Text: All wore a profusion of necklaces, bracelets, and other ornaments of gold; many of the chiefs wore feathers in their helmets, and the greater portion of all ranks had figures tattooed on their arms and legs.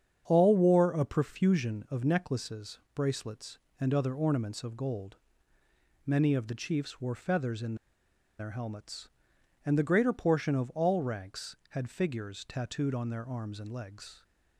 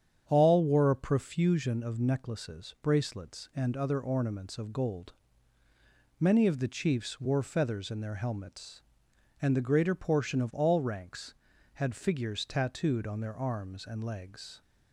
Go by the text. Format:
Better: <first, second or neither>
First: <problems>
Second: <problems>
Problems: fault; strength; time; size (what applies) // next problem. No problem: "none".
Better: second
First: starts louder than the rest; strong; until 1.2 s; 8 dB // pauses between "in" and "their"; noticeable; at 7.7 s; 0.62 s long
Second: starts louder than the rest; strong; until 1.2 s; 8.5 dB